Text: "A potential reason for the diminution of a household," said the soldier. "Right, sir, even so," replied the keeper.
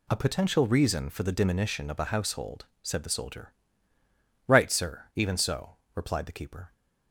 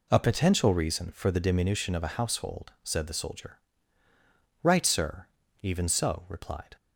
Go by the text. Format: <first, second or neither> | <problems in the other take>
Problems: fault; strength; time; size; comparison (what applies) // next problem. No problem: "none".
first | stops before "the keeper"; at 6.7 s